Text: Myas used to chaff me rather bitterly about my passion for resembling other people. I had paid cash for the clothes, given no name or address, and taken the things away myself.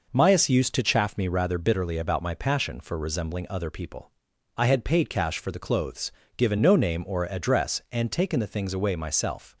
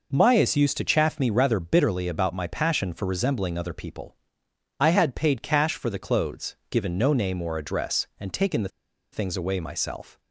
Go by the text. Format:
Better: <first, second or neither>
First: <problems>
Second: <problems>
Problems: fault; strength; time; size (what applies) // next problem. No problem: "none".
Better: first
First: none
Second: pauses between "the" and "things"; at 8.6 s; 0.42 s long